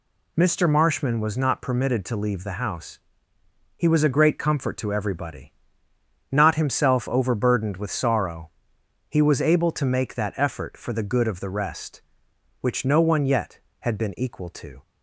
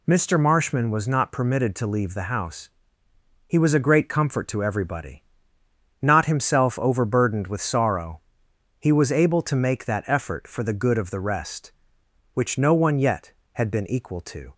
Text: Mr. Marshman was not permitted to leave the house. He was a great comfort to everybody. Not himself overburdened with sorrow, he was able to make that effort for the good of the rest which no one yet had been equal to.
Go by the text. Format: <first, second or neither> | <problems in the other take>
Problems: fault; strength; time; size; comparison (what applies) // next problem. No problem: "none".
neither | none